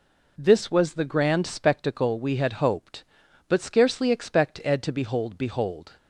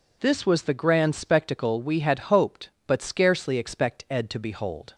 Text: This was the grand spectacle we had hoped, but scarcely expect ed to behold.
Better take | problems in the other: second | says "behold" twice; at 5.3 s

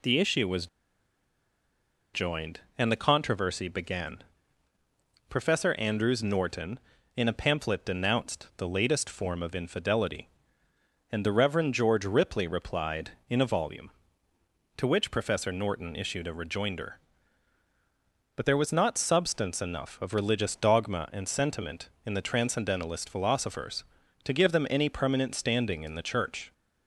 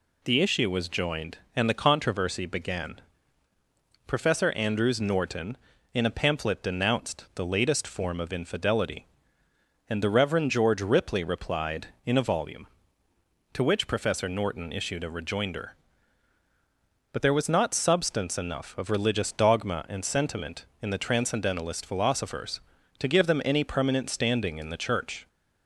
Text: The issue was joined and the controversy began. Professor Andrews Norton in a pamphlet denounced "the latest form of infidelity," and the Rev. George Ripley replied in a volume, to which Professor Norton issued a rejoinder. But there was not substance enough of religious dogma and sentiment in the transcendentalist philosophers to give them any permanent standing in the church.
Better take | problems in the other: second | pauses between "was" and "joined"; strong; at 0.6 s; 1.4 s long

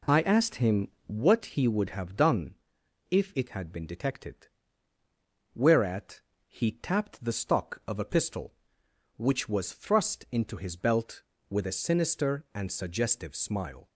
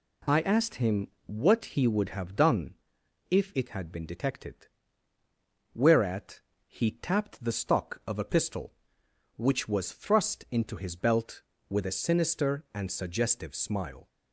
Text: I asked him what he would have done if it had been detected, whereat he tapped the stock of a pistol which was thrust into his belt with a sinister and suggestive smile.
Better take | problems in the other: second | starts louder than the rest; slight; until 1.4 s; 2.5 dB // pauses between "him" and "what"; slight; at 0.8 s; 0.16 s long; slight in the second // pauses between "done" and "if"; noticeable; at 2.5 s; 0.54 s long; noticeable in the second // pauses between "whereat" and "he"; slight; at 6.1 s; 0.26 s long; slight in the second

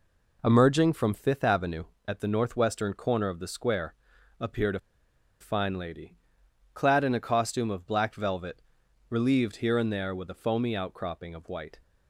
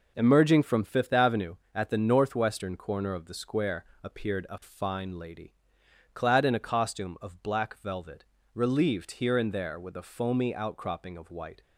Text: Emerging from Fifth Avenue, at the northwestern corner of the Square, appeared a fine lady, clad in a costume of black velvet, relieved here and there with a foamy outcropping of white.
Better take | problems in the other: second | pauses between "a" and "fine"; noticeable; at 4.7 s; 0.62 s long

